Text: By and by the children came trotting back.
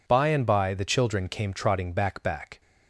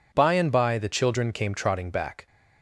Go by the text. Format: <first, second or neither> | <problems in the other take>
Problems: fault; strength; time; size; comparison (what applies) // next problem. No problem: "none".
second | says "back" twice; at 2.2 s